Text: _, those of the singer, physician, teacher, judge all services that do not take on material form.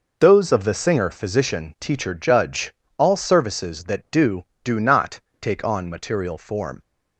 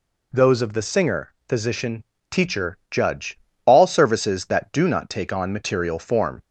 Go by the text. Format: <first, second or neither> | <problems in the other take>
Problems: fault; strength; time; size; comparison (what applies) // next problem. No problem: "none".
second | pauses between "judge" and "all"; slight; at 2.7 s; 0.24 s long; slight in the second // says "do" twice; at 4.6 s // pauses between "not" and "take"; slight; at 5.1 s; 0.23 s long